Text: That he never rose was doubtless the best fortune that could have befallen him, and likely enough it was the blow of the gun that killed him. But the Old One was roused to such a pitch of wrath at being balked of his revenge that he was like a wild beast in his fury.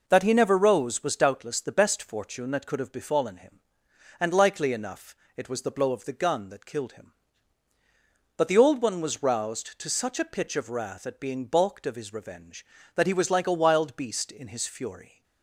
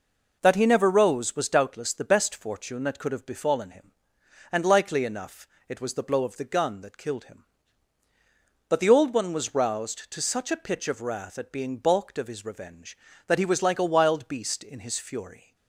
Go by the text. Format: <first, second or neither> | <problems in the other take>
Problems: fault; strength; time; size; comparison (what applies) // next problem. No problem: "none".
neither | pauses between "enough" and "it"; slight; the same in both